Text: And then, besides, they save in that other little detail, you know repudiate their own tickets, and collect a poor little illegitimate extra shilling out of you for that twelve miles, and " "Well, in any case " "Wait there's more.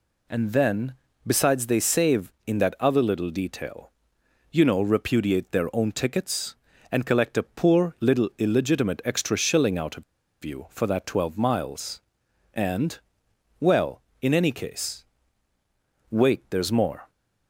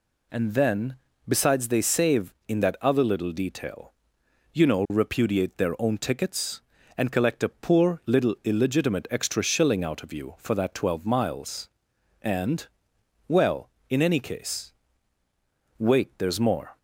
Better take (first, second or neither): second